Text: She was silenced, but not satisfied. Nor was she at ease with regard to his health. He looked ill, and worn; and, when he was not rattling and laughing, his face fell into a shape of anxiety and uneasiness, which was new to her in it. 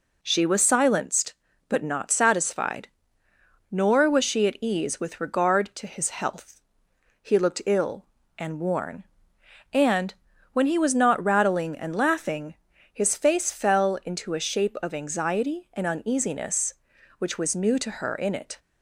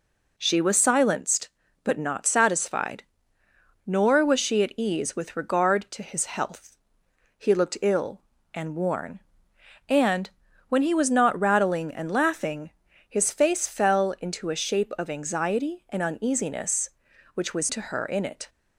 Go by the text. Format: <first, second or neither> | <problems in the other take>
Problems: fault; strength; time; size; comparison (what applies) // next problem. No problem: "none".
first | skips "new"; at 17.6 s